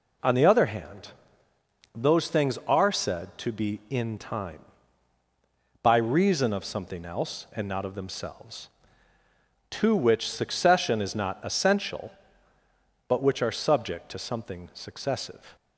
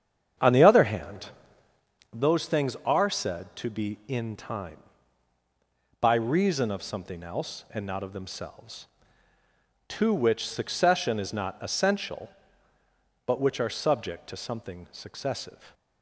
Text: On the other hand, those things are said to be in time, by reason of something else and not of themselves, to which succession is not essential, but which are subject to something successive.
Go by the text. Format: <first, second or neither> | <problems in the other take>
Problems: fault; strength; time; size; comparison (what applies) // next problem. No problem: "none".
first | starts louder than the rest; strong; until 2.0 s; 8 dB